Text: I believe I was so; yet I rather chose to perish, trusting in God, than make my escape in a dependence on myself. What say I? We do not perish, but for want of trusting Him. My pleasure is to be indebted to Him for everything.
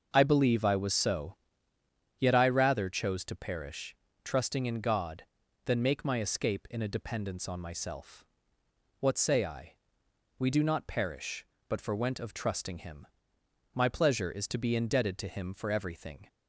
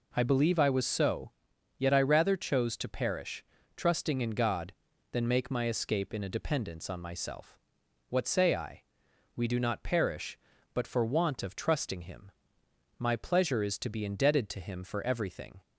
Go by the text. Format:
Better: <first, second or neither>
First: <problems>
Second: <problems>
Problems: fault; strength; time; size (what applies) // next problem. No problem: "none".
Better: second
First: starts louder than the rest; until 1.1 s; 6 dB // says "went" for "want"; at 11.9 s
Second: none